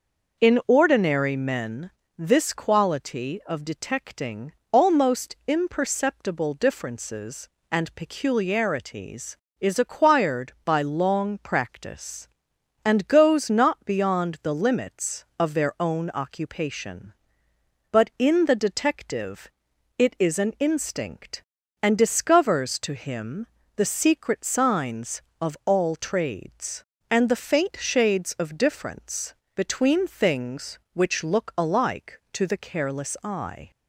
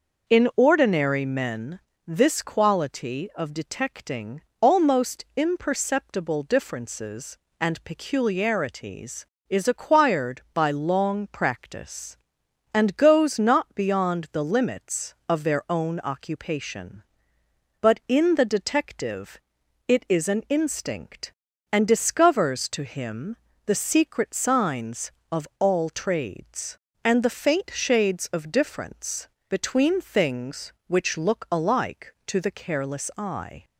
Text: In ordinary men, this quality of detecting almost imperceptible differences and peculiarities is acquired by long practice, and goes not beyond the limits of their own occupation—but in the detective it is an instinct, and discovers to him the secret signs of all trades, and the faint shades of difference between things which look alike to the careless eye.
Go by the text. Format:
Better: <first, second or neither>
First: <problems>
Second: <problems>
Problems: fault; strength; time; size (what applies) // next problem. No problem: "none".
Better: neither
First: pauses between "detecting" and "almost"; slight; at 4.5 s; 0.18 s long // pauses between "detective" and "it"; noticeable; at 19.4 s; 0.48 s long // pauses between "him" and "the"; slight; at 23.4 s; 0.28 s long // pauses between "difference" and "between"; slight; at 29.3 s; 0.22 s long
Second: pauses between "detecting" and "almost"; slight; at 4.4 s; 0.18 s long // pauses between "detective" and "it"; noticeable; at 19.3 s; 0.48 s long // pauses between "him" and "the"; slight; at 23.3 s; 0.28 s long // pauses between "difference" and "between"; slight; at 29.2 s; 0.22 s long